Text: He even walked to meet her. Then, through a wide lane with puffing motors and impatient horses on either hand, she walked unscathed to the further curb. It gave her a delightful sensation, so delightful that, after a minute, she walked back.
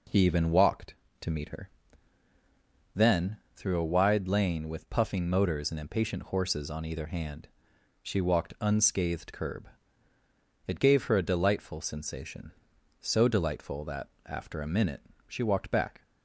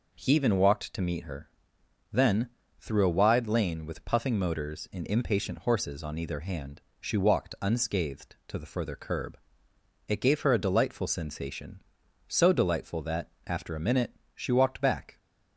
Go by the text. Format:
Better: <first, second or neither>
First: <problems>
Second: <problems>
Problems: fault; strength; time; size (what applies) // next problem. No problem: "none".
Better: second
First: skips "to the further"; at 9.3 s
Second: none